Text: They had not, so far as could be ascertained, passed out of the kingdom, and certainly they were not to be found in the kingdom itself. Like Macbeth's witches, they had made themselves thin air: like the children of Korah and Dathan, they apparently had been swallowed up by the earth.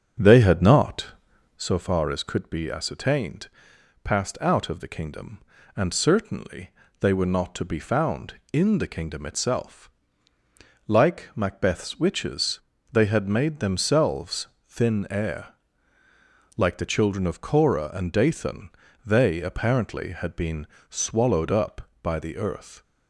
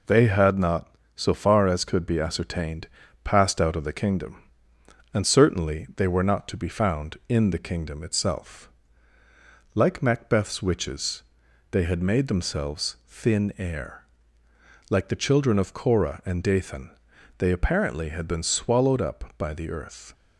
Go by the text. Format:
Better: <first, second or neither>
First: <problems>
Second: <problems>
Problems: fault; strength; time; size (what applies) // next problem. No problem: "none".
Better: second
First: starts louder than the rest; until 1.7 s; 7 dB // pauses between "certainly" and "they"; slight; at 6.7 s; 0.28 s long // pauses between "themselves" and "thin"; slight; at 14.4 s; 0.18 s long // pauses between "been" and "swallowed"; slight; at 20.6 s; 0.24 s long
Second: none